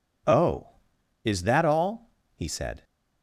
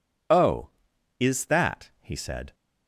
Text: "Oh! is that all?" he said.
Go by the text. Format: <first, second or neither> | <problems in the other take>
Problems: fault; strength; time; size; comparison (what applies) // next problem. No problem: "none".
first | skips "all"; at 1.9 s